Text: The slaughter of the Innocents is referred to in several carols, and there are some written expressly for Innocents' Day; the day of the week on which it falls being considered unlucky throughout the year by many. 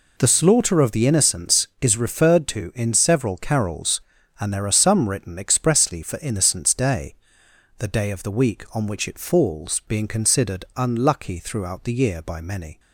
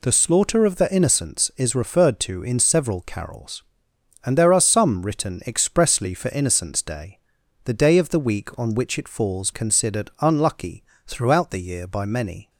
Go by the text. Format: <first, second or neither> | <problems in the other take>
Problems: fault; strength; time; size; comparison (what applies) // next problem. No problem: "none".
first | skips "being"; at 9.5 s // pauses between "unlucky" and "throughout"; slight; at 10.8 s; 0.22 s long